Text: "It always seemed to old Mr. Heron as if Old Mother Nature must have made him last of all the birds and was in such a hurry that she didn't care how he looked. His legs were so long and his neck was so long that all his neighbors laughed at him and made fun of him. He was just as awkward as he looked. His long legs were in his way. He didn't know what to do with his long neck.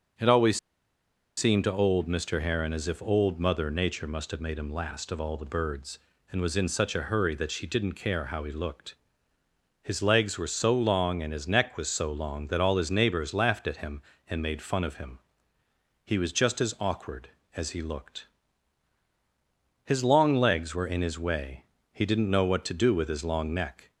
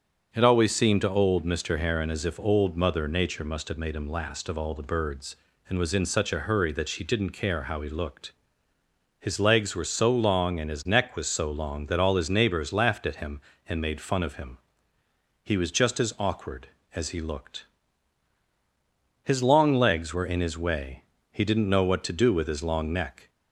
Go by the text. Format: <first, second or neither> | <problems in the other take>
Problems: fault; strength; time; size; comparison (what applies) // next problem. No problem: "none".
second | pauses between "always" and "seemed"; noticeable; at 0.5 s; 0.78 s long